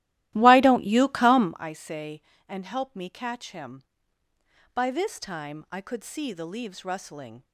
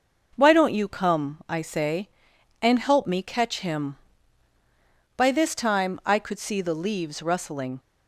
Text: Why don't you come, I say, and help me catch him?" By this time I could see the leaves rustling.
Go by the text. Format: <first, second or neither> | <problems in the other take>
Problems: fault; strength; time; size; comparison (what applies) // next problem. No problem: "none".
second | starts louder than the rest; strong; until 1.6 s; 15.5 dB